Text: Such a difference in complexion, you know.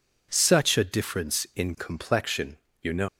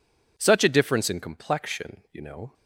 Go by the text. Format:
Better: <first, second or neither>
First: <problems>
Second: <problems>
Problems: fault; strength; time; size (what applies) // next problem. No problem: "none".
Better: second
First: leaves "know" unfinished; at 3.0 s; 125 ms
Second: none